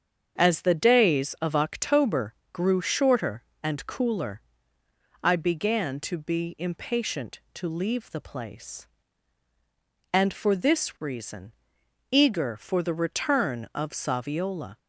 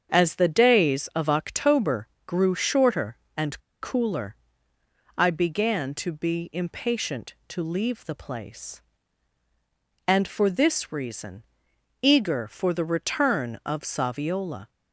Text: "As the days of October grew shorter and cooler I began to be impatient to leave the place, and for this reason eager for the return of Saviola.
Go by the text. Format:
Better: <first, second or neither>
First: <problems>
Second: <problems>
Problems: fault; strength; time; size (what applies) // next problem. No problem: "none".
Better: first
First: starts louder than the rest; strong; until 1.4 s; 7 dB // pauses between "October" and "grew"; slight; at 2.3 s; 0.18 s long // pauses between "cooler" and "I"; noticeable; at 4.4 s; 0.82 s long // pauses between "reason" and "eager"; noticeable; at 11.5 s; 0.58 s long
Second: starts louder than the rest; strong; until 1.1 s; 7 dB // pauses between "October" and "grew"; slight; at 2.0 s; 0.18 s long // pauses between "and" and "cooler"; slight; at 3.5 s; 0.23 s long // pauses between "cooler" and "I"; noticeable; at 4.3 s; 0.82 s long // pauses between "reason" and "eager"; noticeable; at 11.4 s; 0.58 s long